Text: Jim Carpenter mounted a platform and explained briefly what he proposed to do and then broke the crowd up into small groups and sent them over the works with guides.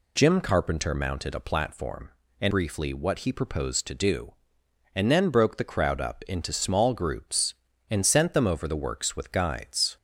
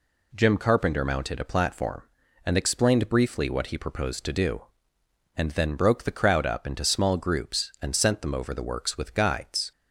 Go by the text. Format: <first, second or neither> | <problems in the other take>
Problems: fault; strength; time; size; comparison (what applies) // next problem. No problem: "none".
second | skips "explained"; at 2.5 s